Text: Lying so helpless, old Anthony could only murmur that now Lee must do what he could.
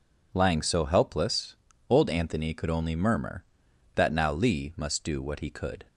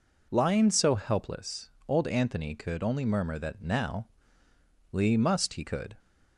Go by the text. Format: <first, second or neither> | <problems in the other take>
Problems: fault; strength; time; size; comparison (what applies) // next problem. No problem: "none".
first | pauses between "now" and "Lee"; noticeable; at 4.0 s; 0.82 s long // skips "do what"; at 5.5 s